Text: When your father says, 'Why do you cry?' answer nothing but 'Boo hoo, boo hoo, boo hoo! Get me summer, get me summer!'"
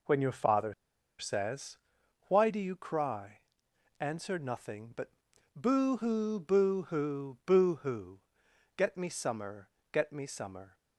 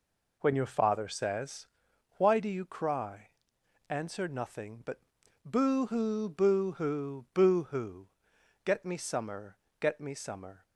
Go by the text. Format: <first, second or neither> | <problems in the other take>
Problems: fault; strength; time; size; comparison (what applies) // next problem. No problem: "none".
second | pauses between "father" and "says"; at 0.7 s; 0.45 s long // pauses between "but" and "Boo"; at 5.1 s; 0.42 s long; also in the second